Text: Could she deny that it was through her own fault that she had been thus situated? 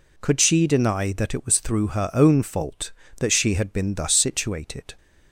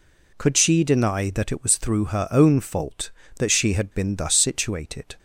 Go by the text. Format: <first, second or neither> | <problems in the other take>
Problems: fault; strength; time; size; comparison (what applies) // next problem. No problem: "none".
neither | none